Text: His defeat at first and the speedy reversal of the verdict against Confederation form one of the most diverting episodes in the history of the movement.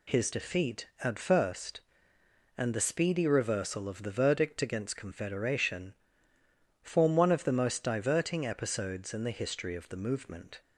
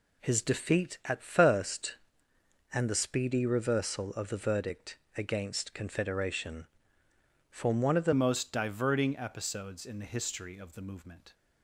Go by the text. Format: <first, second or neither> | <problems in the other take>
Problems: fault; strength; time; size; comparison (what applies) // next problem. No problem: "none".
first | pauses between "verdict" and "against"; slight; at 4.9 s; 0.18 s long // pauses between "Confederation" and "form"; noticeable; at 6.6 s; 0.82 s long; noticeable in the first // changes voice at "most"; from 8.1 s on; 3.2 s long